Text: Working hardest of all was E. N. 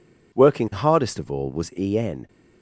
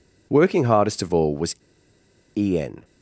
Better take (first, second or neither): first